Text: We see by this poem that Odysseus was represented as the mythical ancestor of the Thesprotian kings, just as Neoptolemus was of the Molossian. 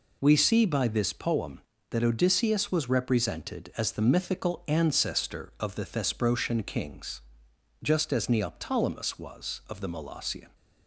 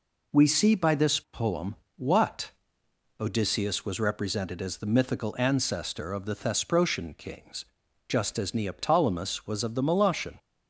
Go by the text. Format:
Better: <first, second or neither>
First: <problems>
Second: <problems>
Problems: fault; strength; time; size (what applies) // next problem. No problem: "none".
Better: first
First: none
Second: says "what" for "that"; at 1.9 s